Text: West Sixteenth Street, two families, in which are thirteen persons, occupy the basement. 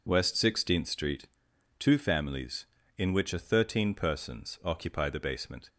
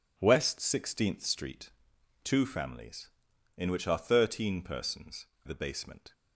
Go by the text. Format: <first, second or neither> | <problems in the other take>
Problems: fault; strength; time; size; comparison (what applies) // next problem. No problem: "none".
first | skips "occupy"; at 5.3 s